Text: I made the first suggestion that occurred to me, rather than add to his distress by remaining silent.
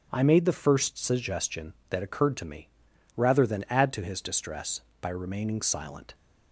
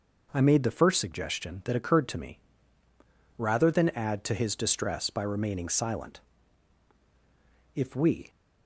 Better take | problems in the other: first | goes on to say "If we"; from 7.7 s on; 0.56 s long

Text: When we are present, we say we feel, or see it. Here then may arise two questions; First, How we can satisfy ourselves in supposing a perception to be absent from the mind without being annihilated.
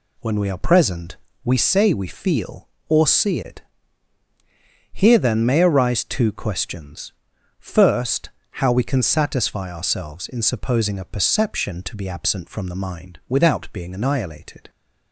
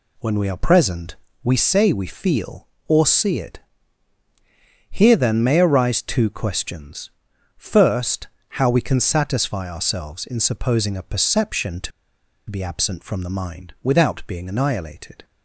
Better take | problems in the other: first | pauses between "to" and "be"; noticeable; at 11.9 s; 0.59 s long

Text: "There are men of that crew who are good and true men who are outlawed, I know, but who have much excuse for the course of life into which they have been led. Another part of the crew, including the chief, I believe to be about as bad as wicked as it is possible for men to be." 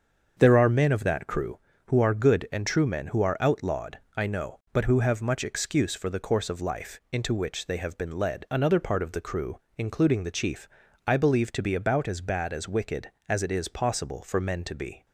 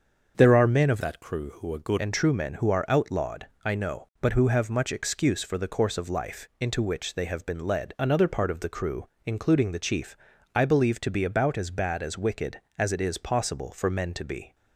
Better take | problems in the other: first | starts louder than the rest; until 1.3 s; 6.5 dB; also in the first // changes voice from "that" to "good"; from 1.0 to 1.9 s; 0.9 s long

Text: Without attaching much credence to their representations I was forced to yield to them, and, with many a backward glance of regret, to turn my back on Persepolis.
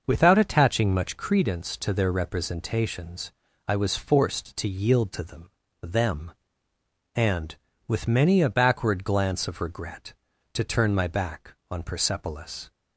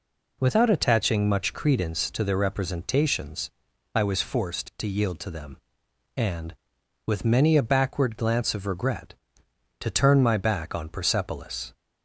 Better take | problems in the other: second | starts louder than the rest; noticeable; until 1.0 s; 6 dB // pauses between "representations" and "I"; slight; at 3.3 s; 0.34 s long; also in the second // says "them" twice; at 5.8 s

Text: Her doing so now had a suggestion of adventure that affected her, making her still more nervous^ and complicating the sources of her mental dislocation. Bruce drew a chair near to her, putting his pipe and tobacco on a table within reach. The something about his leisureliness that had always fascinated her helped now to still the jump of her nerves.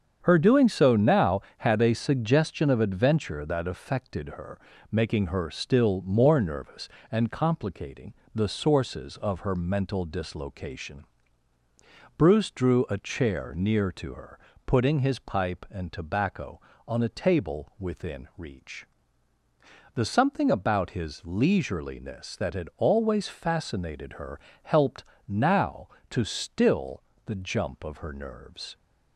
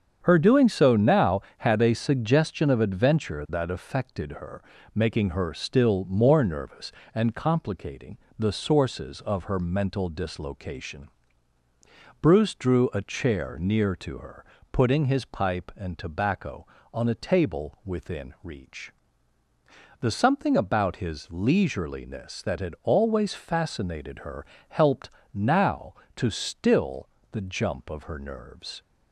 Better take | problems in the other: neither | starts louder than the rest; strong; the same in both // pauses between "complicating" and "the"; slight; the same in both // pauses between "her" and "helped"; slight; the same in both // pauses between "helped" and "now"; slight; the same in both // pauses between "still" and "the"; slight; the same in both

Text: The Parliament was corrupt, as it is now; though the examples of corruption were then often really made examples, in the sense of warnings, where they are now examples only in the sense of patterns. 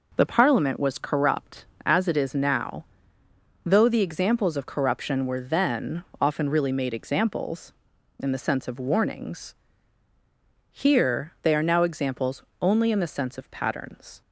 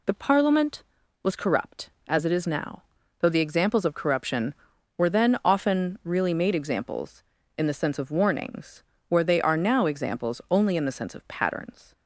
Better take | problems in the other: second | pauses between "then" and "often"; slight; at 6.0 s; 0.18 s long // says "here" for "where"; at 10.7 s // pauses between "examples" and "only"; slight; at 12.4 s; 0.18 s long

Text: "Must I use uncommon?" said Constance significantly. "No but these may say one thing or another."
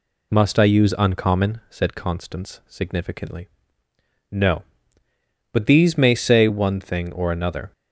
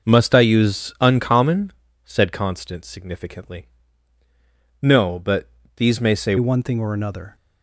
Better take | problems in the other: first | pauses between "but" and "these"; slight; at 5.4 s; 0.28 s long // changes voice at "one"; from 6.3 s on; 1.0 s long

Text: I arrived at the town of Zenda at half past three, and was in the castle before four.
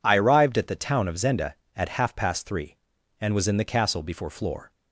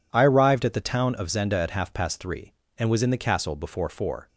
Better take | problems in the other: second | says "floor" for "four"; at 4.3 s

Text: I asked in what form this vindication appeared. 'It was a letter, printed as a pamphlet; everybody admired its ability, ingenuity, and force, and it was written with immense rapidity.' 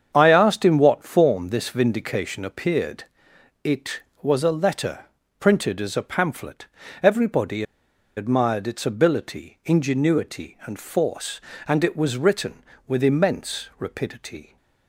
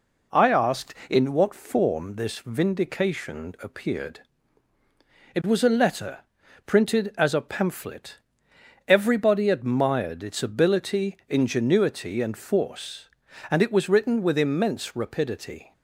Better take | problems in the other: second | starts louder than the rest; strong; until 1.1 s; 7.5 dB // pauses between "everybody" and "admired"; noticeable; at 7.6 s; 0.54 s long

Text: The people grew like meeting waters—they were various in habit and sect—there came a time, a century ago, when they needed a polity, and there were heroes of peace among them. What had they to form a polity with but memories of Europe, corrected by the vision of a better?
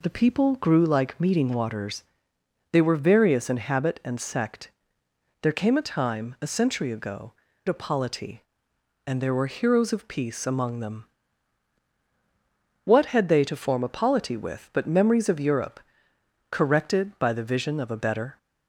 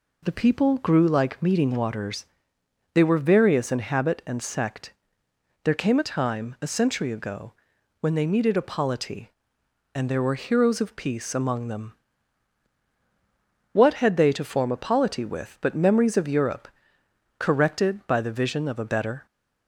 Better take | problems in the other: second | skips "when they needed"; at 7.5 s

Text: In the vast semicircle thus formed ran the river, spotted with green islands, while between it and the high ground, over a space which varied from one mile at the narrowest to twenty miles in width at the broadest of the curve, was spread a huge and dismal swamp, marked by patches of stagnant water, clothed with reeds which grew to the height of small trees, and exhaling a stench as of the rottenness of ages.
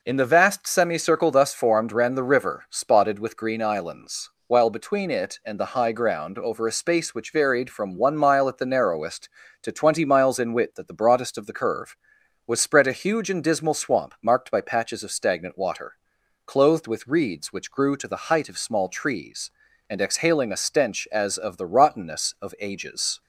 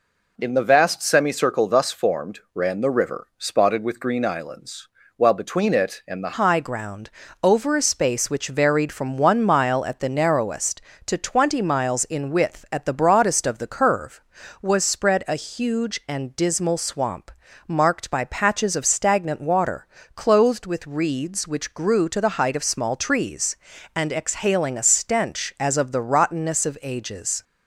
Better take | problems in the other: first | changes voice at "high"; from 6.3 s on; 21.1 s long

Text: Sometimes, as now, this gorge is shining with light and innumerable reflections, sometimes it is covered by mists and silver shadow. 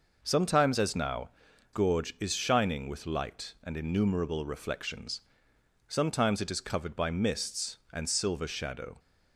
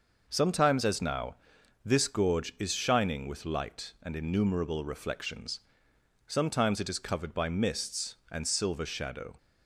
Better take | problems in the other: second | skips "this"; at 1.5 s

